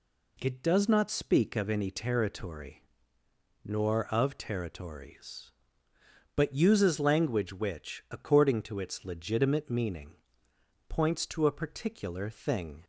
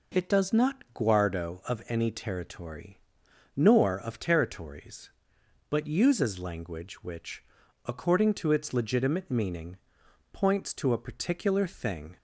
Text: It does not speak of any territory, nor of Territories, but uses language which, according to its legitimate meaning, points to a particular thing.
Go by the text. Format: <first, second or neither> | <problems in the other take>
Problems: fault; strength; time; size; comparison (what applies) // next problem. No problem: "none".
first | says "guardo" for "speak"; at 0.9 s